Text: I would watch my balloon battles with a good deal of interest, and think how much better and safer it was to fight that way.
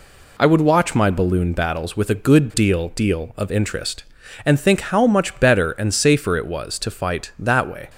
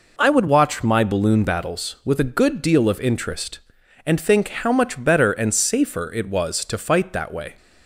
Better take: second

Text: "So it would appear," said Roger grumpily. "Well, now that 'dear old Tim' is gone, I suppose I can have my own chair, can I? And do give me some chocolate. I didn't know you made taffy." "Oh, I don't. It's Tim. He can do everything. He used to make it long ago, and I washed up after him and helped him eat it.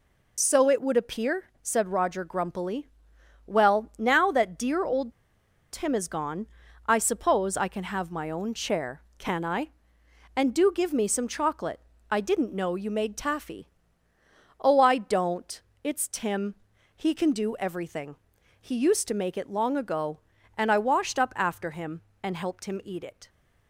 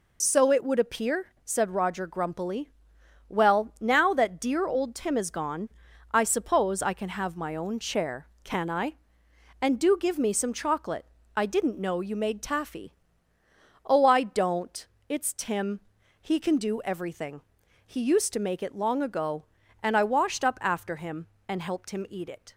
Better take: second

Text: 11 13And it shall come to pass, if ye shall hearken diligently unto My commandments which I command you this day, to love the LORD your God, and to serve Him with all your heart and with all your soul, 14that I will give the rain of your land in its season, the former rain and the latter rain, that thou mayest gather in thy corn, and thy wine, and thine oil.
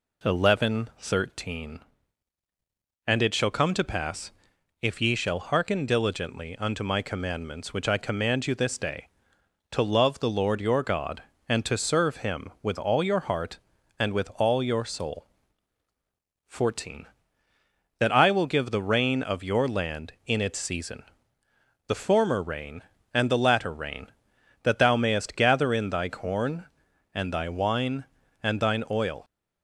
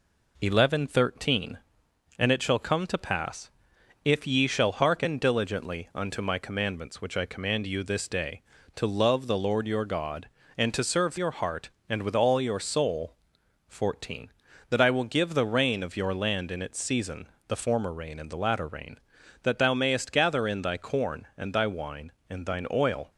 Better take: first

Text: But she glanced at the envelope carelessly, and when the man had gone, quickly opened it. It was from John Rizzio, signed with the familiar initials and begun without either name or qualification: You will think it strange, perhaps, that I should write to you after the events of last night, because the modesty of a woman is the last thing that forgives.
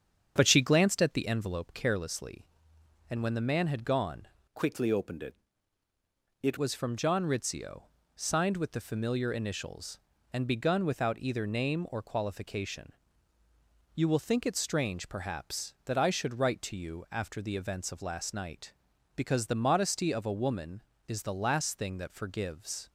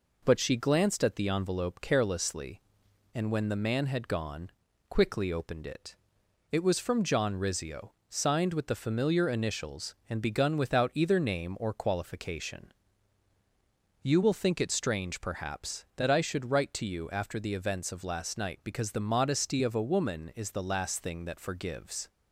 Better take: second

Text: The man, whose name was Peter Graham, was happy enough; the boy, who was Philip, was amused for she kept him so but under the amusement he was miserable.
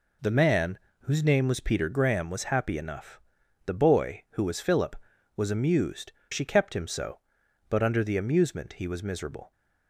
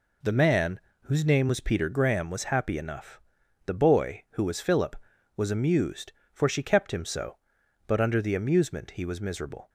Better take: second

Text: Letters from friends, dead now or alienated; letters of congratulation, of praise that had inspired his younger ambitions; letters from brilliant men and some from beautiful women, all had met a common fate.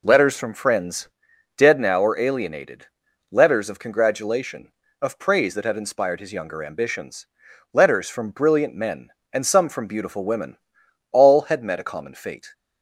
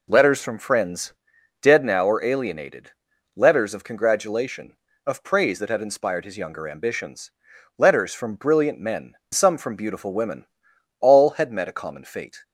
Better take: first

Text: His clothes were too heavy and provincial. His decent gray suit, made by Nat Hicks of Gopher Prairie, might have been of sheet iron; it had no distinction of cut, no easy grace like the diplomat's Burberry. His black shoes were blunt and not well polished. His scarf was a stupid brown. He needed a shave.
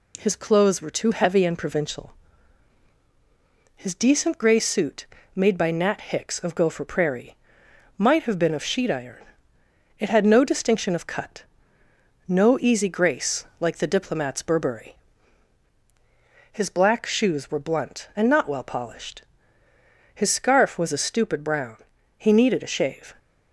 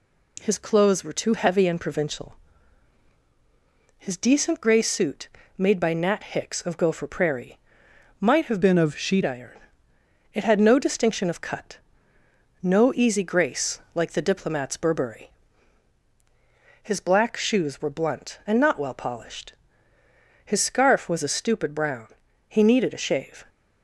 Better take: first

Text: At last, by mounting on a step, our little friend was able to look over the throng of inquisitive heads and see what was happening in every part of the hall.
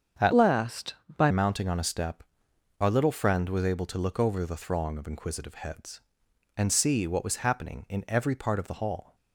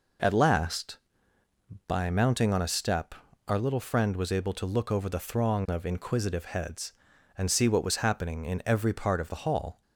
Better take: second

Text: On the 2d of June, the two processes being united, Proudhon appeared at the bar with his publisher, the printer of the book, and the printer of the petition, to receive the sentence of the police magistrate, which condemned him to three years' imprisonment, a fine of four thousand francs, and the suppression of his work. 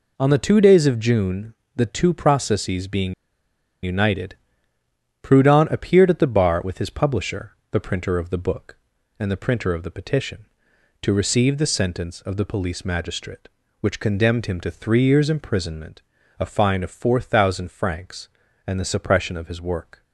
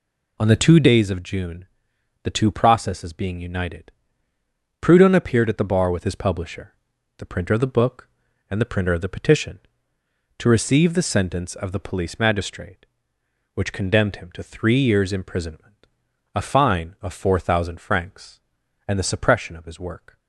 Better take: second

